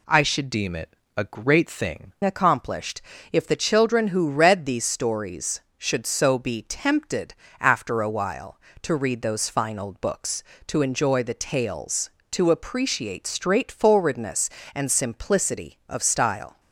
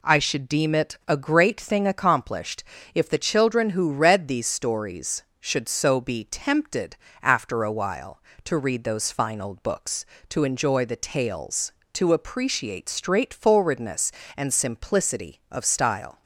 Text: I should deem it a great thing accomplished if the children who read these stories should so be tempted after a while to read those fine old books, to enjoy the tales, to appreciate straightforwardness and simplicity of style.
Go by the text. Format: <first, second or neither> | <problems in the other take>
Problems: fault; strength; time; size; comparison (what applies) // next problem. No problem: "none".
second | changes voice from "deem" to "thing"; from 0.5 to 2.1 s; 1.6 s long // pauses between "it" and "a"; slight; at 0.9 s; 0.22 s long // pauses between "accomplished" and "if"; slight; at 3.0 s; 0.30 s long; slight in the second // pauses between "tempted" and "after"; slight; at 7.3 s; 0.26 s long; slight in the second